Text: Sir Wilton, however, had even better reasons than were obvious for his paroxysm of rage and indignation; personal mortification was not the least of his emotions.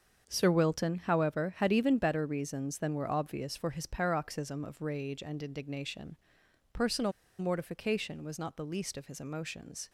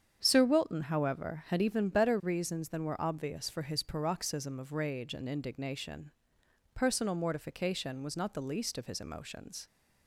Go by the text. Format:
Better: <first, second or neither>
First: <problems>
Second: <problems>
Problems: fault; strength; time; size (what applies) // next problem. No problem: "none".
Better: second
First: starts louder than the rest; until 1.2 s; 7 dB // pauses between "personal" and "mortification"; slight; at 7.1 s; 0.27 s long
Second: starts louder than the rest; strong; until 1.2 s; 8 dB